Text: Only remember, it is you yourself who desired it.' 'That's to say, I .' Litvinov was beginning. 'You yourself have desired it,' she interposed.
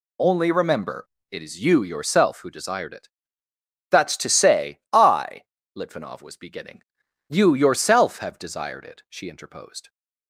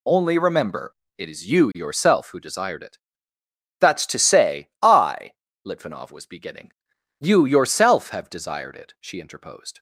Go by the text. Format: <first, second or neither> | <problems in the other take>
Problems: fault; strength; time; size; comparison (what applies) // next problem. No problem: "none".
neither | none